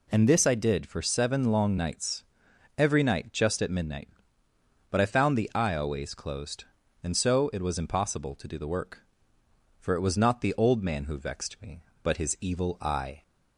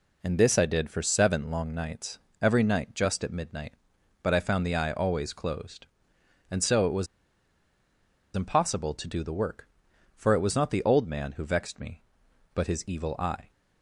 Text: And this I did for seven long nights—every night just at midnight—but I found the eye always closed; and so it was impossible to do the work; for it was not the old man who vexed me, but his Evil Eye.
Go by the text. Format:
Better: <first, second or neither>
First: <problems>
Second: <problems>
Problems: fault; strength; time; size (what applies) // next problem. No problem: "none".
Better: first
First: none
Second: pauses between "was" and "impossible"; strong; at 7.0 s; 1.2 s long